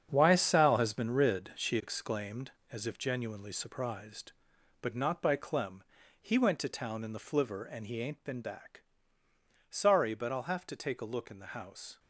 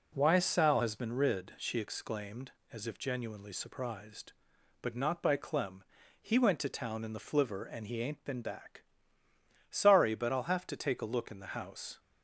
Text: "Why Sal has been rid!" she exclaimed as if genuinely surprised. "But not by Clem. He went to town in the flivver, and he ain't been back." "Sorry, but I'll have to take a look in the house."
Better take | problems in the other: second | gets quieter; strong; throughout; 10 dB

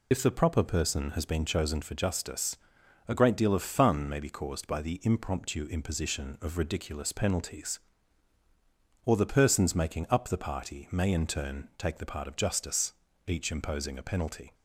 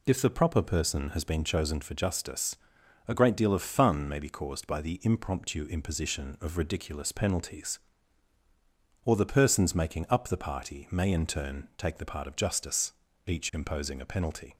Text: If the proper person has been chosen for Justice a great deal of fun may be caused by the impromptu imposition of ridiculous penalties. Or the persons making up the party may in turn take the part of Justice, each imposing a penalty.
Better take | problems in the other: second | loses the start of "If"; at 0.1 s; 45 ms // pauses between "Justice" and "a"; noticeable; at 2.5 s; 0.50 s long; noticeable in the second

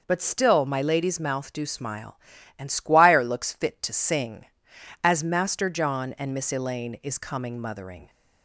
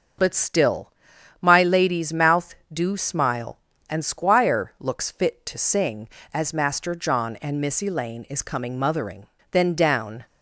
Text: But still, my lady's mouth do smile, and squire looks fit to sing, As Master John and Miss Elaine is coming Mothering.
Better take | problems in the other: first | starts louder than the rest; until 1.6 s; 6.5 dB // goes on to say "Then down"; noticeable; from 9.5 s on; 0.74 s long

